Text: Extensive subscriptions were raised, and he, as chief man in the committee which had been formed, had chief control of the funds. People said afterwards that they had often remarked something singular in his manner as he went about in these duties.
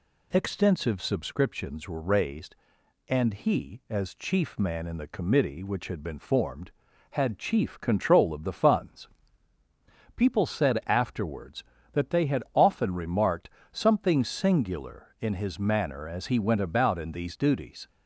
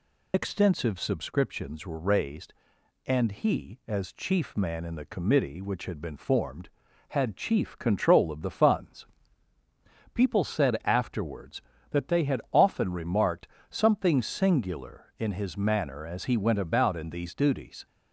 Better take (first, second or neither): first